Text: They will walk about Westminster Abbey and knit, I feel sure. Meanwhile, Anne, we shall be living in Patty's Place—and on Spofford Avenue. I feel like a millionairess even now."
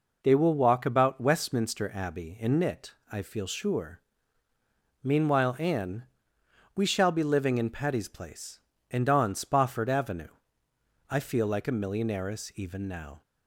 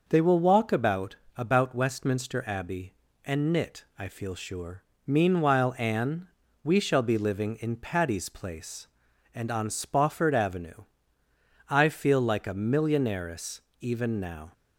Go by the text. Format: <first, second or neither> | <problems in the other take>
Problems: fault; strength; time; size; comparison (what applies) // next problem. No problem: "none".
first | says "about" twice; at 1.3 s // pauses between "millionairess" and "even"; slight; at 13.6 s; 0.20 s long